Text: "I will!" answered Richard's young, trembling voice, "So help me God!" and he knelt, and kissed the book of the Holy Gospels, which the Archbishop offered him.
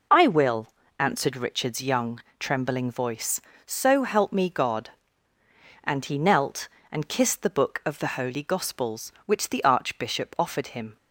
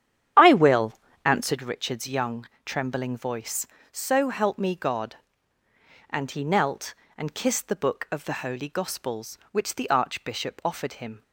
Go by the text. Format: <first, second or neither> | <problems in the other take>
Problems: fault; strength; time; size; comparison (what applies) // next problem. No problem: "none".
first | starts louder than the rest; strong; until 1.5 s; 9.5 dB